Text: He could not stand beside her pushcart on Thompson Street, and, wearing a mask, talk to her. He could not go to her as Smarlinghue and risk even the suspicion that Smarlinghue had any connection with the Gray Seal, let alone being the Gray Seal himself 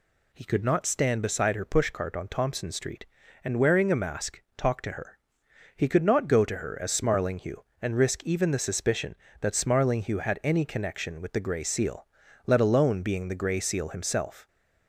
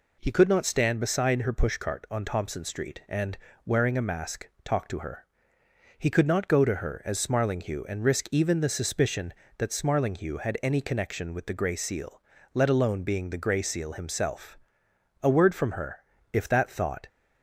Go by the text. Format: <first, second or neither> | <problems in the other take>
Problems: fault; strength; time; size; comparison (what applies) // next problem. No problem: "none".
first | goes on to say "A word from her if that thought"; strong; from 15.2 s on; 1.8 s long